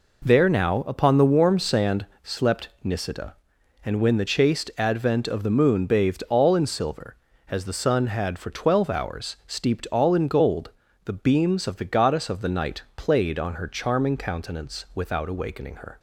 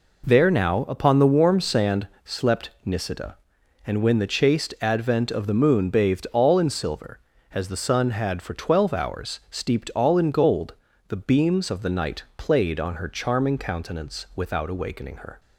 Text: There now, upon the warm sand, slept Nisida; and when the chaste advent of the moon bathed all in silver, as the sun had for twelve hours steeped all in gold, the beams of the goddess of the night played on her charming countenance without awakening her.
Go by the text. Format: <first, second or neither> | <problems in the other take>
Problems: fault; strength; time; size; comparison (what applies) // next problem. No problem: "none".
first | skips "of the goddess"; at 11.6 s